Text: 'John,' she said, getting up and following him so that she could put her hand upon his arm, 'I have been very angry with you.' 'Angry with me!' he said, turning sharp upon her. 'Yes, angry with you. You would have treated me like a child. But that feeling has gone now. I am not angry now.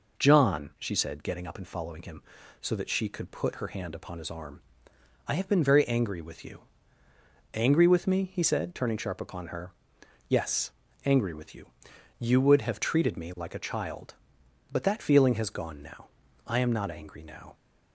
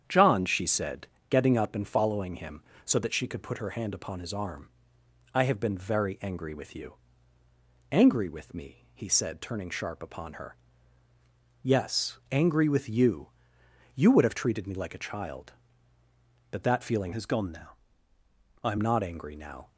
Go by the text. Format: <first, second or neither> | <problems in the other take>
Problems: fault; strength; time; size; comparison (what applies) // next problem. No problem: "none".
first | starts louder than the rest; strong; until 1.0 s; 8.5 dB // changes voice from "has" to "am"; from 17.1 to 18.7 s; 1.6 s long